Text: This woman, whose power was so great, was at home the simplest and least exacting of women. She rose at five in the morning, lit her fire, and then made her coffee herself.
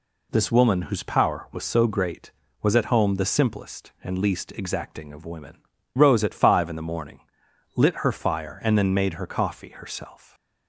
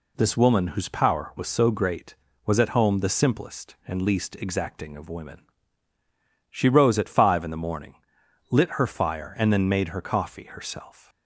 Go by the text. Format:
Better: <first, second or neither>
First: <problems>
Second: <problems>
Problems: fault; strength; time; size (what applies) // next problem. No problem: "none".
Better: second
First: skips "She"; at 5.7 s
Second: none